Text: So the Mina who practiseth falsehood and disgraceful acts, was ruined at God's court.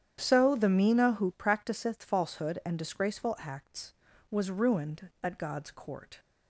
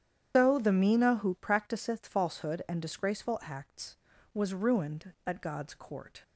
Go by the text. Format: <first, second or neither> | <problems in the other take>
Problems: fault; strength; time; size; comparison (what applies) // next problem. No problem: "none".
first | loses the start of "So"; at 0.3 s; 135 ms // starts louder than the rest; strong; until 1.3 s; 9.5 dB; strong in the first